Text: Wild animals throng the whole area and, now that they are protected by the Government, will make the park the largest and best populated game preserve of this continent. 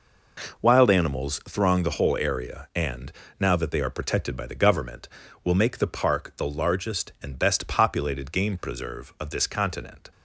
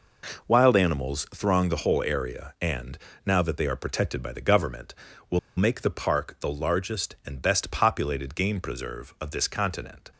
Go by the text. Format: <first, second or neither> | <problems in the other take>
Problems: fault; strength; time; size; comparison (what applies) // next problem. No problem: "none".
first | pauses between "will" and "make"; slight; at 5.3 s; 0.18 s long